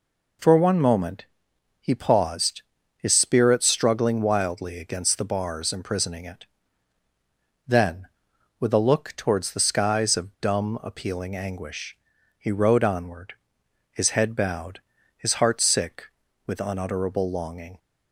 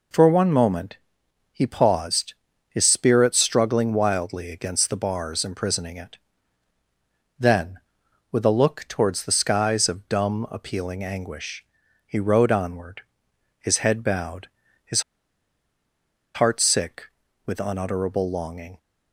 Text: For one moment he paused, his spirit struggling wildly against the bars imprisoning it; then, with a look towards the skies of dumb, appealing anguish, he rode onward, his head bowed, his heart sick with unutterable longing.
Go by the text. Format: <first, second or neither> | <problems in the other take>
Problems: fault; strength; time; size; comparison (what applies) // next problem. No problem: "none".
first | pauses between "moment" and "he"; noticeable; at 0.9 s; 0.56 s long; noticeable in the first // pauses between "his" and "heart"; strong; at 15.0 s; 1.3 s long